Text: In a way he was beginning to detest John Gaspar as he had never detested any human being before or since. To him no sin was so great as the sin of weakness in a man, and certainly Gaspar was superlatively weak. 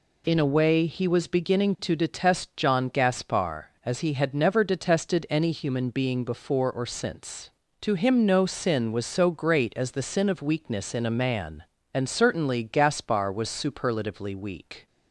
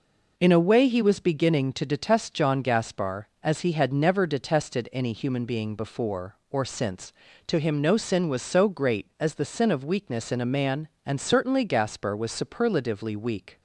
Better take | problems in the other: neither | none

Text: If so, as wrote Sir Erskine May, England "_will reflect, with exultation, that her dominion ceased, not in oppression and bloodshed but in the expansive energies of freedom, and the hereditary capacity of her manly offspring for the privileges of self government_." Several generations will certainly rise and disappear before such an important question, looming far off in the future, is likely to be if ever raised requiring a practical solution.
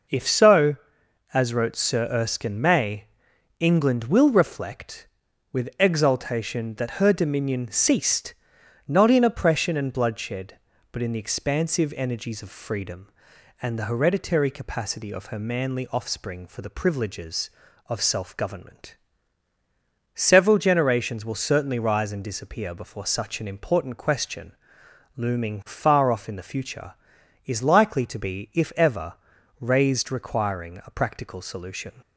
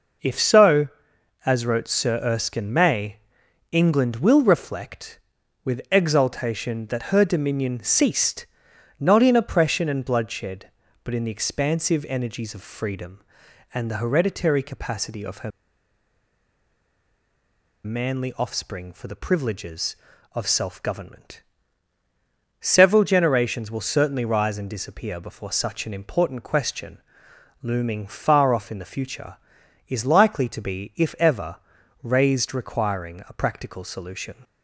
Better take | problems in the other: first | pauses between "her" and "manly"; strong; at 15.5 s; 2.3 s long // pauses between "ever" and "raised"; noticeable; at 31.5 s; 0.46 s long; noticeable in the first

